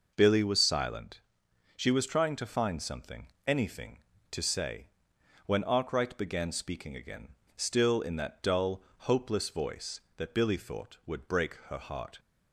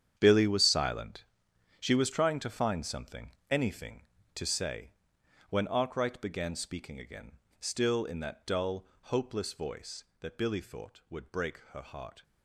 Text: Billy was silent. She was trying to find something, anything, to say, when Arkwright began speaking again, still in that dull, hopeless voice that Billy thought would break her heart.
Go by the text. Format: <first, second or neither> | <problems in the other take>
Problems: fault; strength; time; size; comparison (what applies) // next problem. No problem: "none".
first | gets quieter; strong; throughout; 12.5 dB